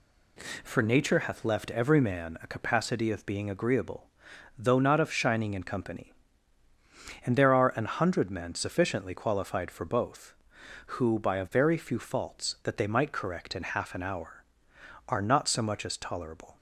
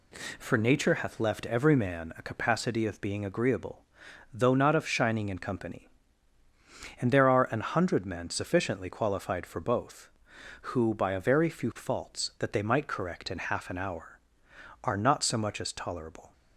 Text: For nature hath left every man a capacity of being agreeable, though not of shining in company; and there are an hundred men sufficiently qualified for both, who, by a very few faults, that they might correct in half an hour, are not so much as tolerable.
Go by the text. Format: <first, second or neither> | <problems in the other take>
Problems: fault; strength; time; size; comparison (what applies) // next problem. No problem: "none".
neither | none